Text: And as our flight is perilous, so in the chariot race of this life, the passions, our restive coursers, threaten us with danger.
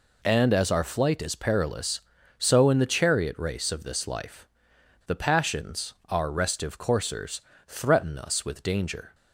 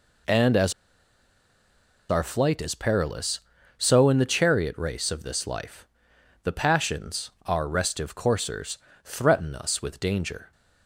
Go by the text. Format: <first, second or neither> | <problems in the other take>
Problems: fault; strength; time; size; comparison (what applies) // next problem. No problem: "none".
first | pauses between "as" and "our"; strong; at 0.7 s; 1.3 s long